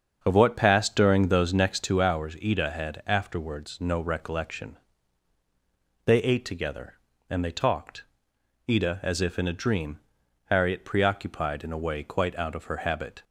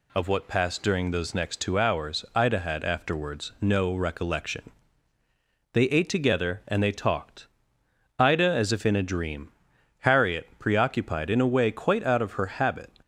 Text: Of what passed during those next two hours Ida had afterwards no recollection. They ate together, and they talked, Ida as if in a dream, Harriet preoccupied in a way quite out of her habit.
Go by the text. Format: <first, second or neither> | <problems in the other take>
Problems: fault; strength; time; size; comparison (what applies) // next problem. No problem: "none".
second | starts louder than the rest; until 1.9 s; 7 dB